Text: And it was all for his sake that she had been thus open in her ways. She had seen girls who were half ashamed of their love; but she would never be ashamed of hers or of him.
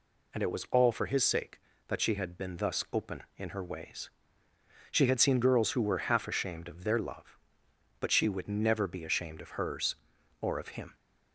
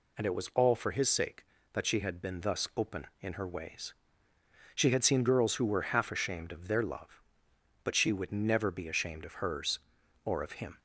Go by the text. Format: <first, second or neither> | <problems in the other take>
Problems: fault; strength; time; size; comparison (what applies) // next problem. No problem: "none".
neither | none